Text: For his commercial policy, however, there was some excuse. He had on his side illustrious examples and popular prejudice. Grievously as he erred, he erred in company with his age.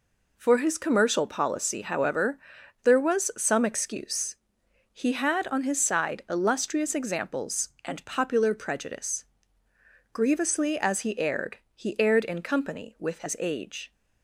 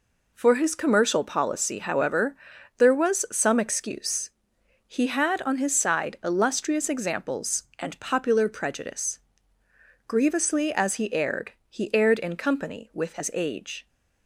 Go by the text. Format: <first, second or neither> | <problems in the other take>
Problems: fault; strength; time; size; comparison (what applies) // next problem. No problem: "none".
neither | none